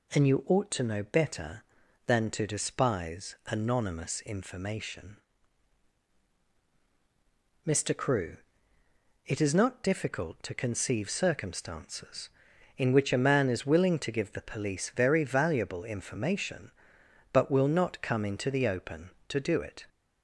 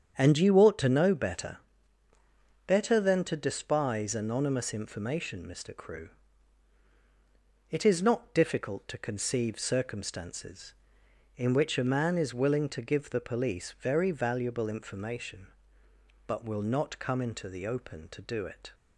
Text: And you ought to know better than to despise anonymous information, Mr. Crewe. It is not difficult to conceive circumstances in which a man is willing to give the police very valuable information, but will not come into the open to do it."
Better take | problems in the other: first | starts louder than the rest; strong; until 1.1 s; 8 dB // says "better" twice; at 2.6 s

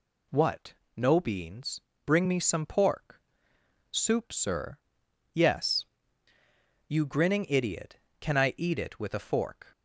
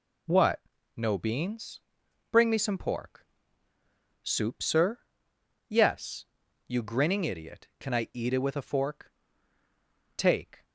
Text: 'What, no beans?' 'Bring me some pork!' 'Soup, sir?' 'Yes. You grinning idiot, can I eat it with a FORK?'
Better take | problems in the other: first | goes on to say "Take"; slight; from 10.1 s on; 0.46 s long

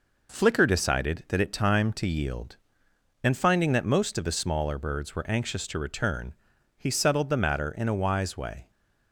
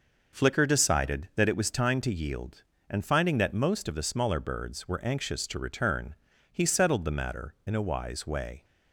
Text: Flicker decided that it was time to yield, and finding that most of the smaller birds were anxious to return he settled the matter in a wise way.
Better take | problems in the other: second | skips "was"; at 1.5 s // pauses between "return" and "he"; noticeable; at 6.3 s; 0.46 s long; slight in the second

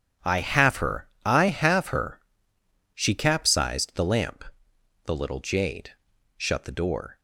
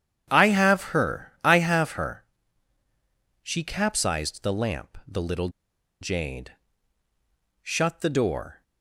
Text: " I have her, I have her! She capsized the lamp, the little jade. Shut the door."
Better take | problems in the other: first | starts louder than the rest; strong; until 1.2 s; 9.5 dB // pauses between "little" and "jade"; noticeable; at 5.4 s; 0.52 s long

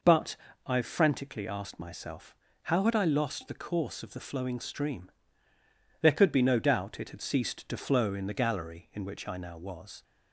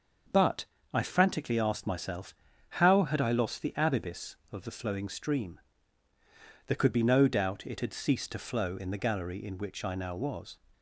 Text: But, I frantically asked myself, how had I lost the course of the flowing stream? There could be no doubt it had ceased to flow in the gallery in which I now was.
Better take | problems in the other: first | starts louder than the rest; until 1.6 s; 6.5 dB // says "abibis" for "course"; at 3.7 s

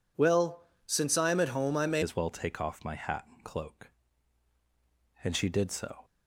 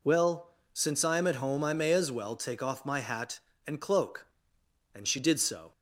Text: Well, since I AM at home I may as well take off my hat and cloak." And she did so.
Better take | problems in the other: second | changes voice at "as"; from 2.0 s on; 4.0 s long

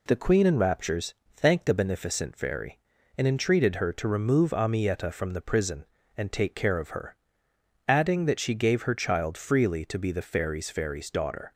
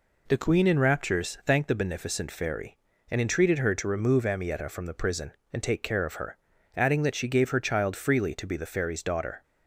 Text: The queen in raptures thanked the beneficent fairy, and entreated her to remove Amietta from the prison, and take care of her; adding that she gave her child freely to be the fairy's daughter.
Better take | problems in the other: second | pauses between "raptures" and "thanked"; slight; at 1.1 s; 0.20 s long // says "fairy's" twice; at 10.7 s

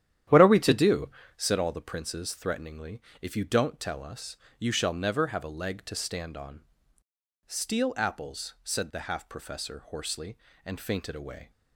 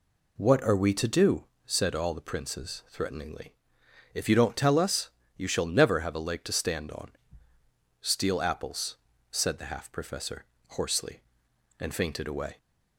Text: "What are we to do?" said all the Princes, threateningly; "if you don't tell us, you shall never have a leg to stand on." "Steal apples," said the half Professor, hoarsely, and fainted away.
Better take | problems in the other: second | starts louder than the rest; strong; until 1.6 s; 11 dB

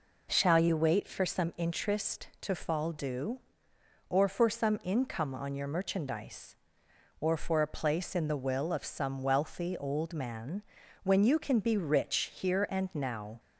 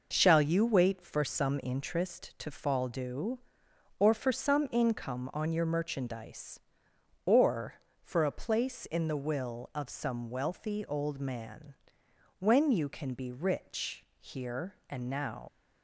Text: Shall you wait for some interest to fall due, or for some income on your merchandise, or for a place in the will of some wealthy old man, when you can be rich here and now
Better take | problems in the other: first | pauses between "rich" and "here"; slight; at 14.0 s; 0.16 s long // leaves "now" unfinished; at 15.4 s; 70 ms

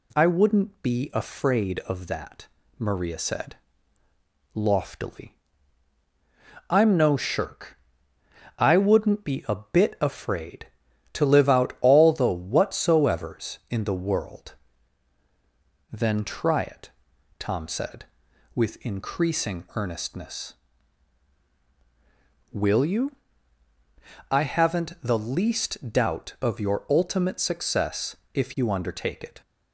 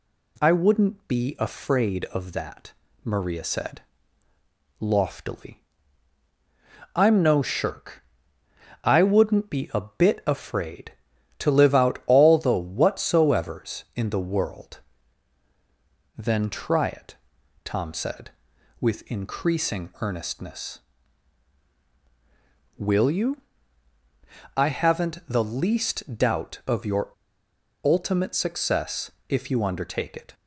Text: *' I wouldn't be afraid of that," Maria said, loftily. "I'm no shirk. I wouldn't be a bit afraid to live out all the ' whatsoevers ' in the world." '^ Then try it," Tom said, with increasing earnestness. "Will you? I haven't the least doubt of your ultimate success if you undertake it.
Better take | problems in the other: first | pauses between "your" and "ultimate"; noticeable; at 27.0 s; 0.75 s long // pauses between "success" and "if"; slight; at 29.1 s; 0.16 s long; slight in the first

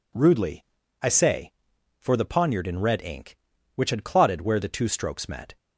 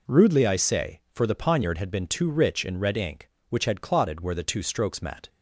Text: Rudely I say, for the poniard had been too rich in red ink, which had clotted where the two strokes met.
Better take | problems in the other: second | pauses between "Rudely" and "I"; at 0.6 s; 0.38 s long // skips "had been too rich"; at 2.6 s

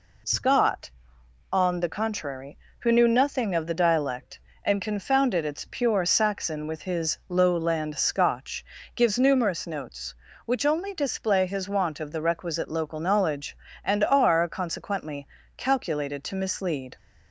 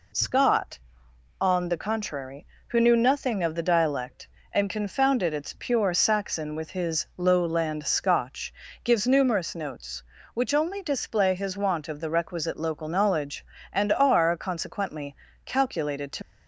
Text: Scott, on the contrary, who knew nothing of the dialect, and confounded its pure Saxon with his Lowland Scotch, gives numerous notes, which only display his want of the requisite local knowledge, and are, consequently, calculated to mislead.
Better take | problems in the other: first | stops before "mislead"; at 16.2 s

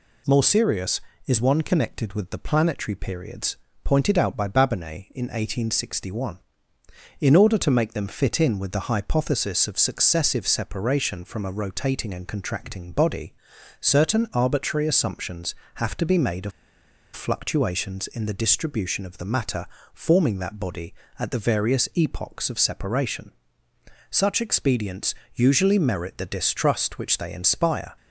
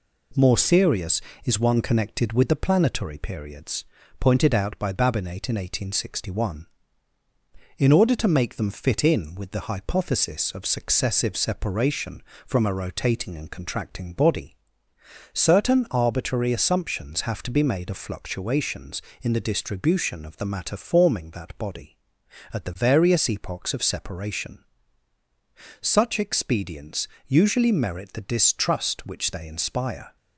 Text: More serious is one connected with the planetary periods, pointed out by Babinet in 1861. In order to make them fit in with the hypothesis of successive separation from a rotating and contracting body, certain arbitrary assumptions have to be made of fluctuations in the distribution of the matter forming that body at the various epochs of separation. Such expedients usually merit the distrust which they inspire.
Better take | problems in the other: second | pauses between "of" and "fluctuations"; noticeable; at 16.5 s; 0.64 s long // pauses between "matter" and "forming"; slight; at 19.6 s; 0.26 s long // pauses between "expedients" and "usually"; slight; at 25.1 s; 0.18 s long; slight in the second

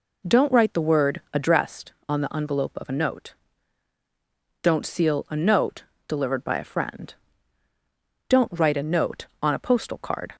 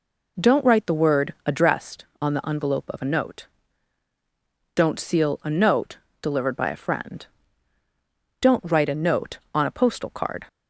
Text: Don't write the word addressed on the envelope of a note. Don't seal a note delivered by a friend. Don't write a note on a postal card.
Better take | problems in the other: neither | pauses between "note" and "delivered"; slight; the same in both

